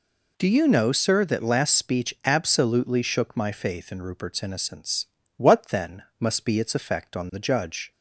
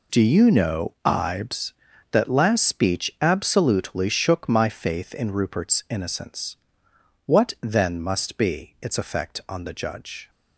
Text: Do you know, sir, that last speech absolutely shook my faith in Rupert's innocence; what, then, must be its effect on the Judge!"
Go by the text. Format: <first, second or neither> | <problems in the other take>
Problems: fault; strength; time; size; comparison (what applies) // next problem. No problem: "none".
first | says "ibes" for "sir"; at 1.0 s